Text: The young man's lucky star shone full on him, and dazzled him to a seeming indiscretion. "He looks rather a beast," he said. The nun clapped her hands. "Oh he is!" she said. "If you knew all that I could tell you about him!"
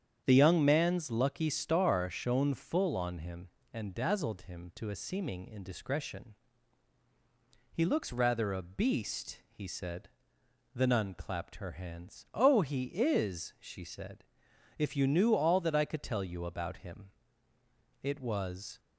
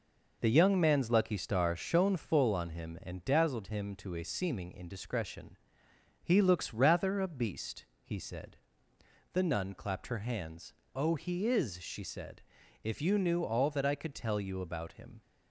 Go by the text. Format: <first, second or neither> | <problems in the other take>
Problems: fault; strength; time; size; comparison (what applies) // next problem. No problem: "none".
second | starts louder than the rest; strong; until 1.2 s; 8.5 dB // goes on to say "It was"; noticeable; from 18.0 s on; 0.78 s long